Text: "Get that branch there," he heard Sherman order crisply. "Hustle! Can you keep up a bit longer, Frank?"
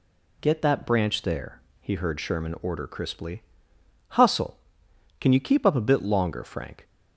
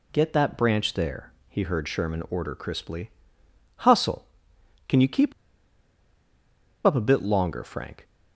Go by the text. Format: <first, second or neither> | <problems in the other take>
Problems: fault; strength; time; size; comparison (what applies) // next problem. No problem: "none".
first | pauses between "keep" and "up"; strong; at 5.3 s; 1.5 s long